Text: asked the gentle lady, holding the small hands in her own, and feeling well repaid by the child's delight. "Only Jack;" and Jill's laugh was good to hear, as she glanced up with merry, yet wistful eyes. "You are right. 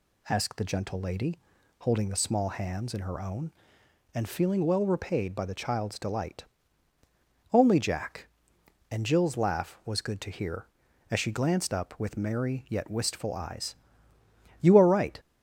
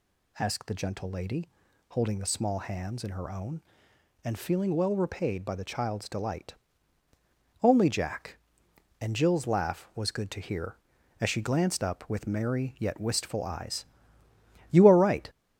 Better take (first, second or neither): first